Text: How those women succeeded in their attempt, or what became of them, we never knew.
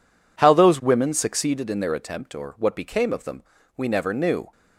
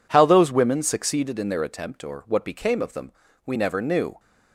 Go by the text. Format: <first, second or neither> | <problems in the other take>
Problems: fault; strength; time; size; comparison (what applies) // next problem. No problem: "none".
neither | none